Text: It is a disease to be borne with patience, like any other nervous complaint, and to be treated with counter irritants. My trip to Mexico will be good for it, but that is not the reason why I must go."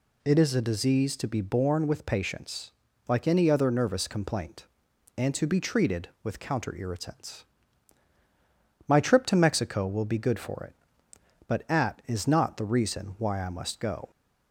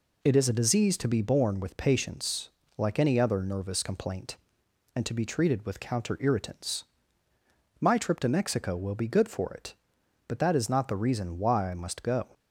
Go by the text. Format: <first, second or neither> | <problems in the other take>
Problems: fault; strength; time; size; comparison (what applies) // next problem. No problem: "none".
second | says "at" for "that"; at 11.7 s